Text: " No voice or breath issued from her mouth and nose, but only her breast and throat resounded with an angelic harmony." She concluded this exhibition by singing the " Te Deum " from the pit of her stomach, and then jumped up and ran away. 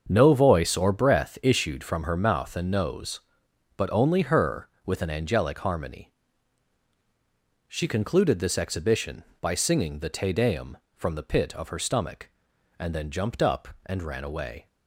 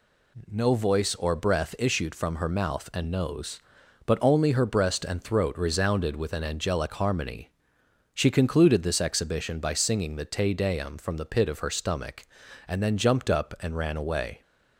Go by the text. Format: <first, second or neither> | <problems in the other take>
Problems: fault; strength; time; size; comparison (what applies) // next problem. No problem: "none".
second | starts louder than the rest; until 1.0 s; 6.5 dB // skips "breast and throat resounded"; at 4.7 s